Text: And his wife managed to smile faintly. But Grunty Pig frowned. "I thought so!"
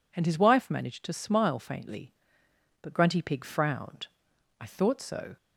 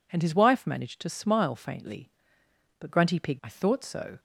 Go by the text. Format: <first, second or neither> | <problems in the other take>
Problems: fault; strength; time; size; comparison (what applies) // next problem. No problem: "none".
first | skips "frowned"; at 3.4 s